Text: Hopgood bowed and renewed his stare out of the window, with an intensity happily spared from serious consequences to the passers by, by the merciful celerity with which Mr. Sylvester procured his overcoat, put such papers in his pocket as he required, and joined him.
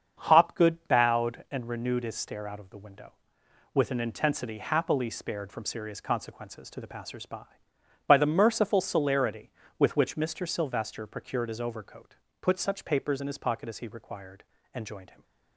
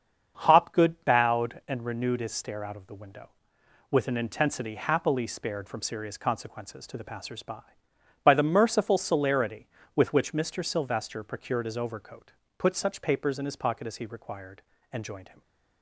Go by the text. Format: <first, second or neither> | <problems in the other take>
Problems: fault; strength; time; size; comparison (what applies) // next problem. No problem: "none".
neither | starts louder than the rest; the same in both